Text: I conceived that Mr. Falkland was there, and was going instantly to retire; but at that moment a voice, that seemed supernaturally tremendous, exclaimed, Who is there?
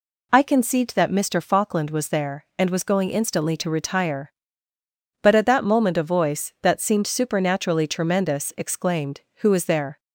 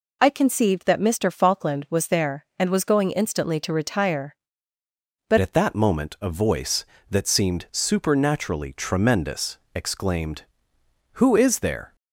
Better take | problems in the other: first | changes voice at "at"; from 5.3 s on; 6.6 s long

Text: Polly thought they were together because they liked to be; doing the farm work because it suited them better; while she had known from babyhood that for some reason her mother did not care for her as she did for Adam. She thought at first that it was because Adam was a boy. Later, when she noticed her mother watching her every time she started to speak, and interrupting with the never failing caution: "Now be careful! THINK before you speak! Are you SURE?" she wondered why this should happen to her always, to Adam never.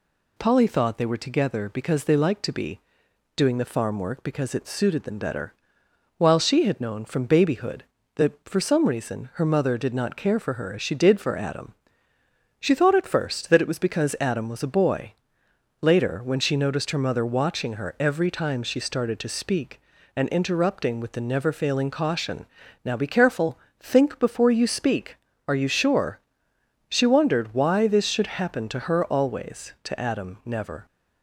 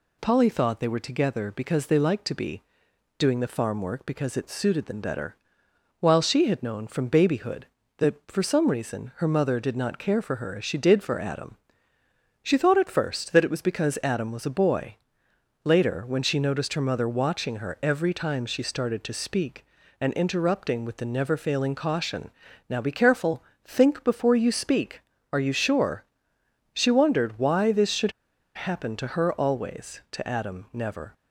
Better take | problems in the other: first | pauses between "should" and "happen"; at 28.1 s; 0.43 s long

